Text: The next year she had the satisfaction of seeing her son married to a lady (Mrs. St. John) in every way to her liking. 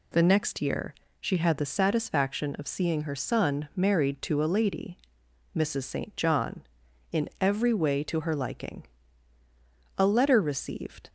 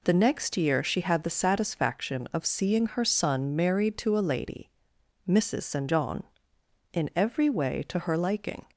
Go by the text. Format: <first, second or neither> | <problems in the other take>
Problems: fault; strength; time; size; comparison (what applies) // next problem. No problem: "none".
second | pauses between "year" and "she"; slight; at 0.9 s; 0.26 s long // goes on to say "A letter received"; noticeable; from 9.9 s on; 1.1 s long